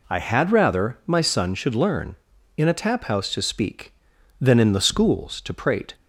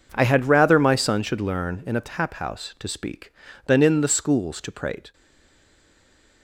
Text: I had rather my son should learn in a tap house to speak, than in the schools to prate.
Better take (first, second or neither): first